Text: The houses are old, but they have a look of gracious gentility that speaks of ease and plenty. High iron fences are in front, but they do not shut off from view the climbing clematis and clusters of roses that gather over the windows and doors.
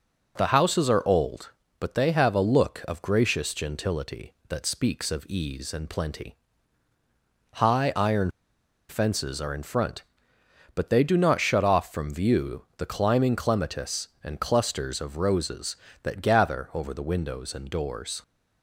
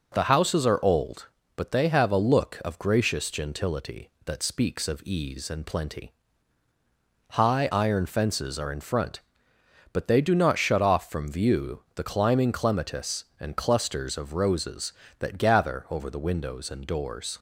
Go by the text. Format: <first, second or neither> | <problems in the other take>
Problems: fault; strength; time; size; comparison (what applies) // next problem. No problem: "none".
second | pauses between "iron" and "fences"; noticeable; at 8.2 s; 0.60 s long